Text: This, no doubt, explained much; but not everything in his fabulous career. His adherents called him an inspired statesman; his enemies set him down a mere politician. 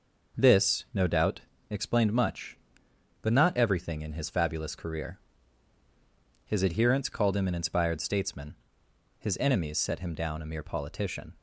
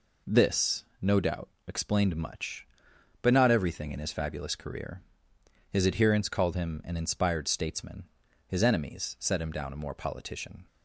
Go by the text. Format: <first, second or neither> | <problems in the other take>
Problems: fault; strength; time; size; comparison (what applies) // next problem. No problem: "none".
first | says "more" for "mere"; at 9.7 s